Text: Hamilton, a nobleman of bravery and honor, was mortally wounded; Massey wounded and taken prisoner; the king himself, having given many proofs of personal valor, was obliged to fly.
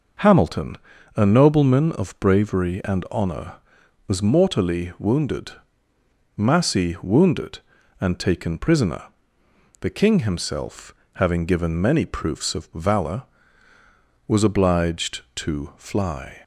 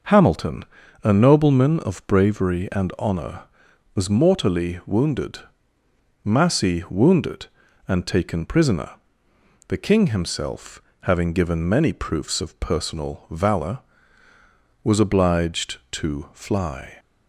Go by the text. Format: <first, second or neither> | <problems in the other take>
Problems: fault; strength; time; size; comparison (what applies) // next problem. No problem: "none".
second | skips "personal"; at 12.7 s